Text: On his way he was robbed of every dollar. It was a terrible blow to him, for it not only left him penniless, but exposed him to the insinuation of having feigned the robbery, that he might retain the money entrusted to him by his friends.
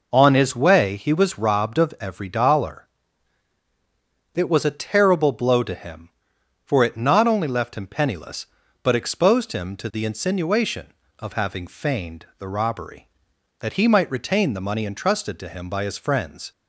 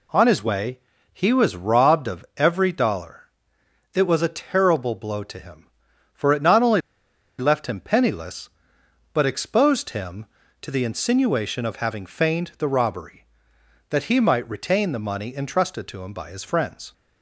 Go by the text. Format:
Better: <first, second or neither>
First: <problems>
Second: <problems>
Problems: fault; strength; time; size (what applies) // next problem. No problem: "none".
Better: first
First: none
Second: pauses between "way" and "he"; slight; at 0.7 s; 0.34 s long // pauses between "only" and "left"; noticeable; at 6.8 s; 0.57 s long